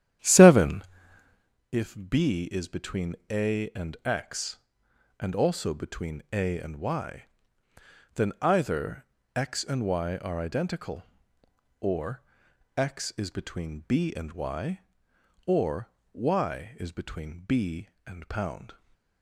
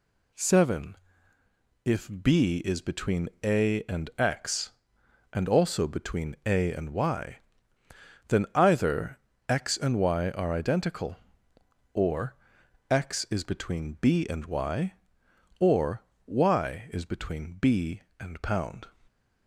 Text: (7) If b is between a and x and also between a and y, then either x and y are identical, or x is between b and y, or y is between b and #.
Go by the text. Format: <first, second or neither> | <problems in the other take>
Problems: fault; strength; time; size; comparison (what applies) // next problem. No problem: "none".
second | starts louder than the rest; strong; until 1.6 s; 11 dB // pauses between "either" and "x"; slight; at 9.0 s; 0.28 s long; slight in the second // pauses between "or" and "x"; noticeable; at 12.2 s; 0.54 s long; noticeable in the second // pauses between "or" and "y"; slight; at 15.8 s; 0.24 s long; slight in the second // stays silent after the last word; slight; from 18.7 s on; 0.5 s long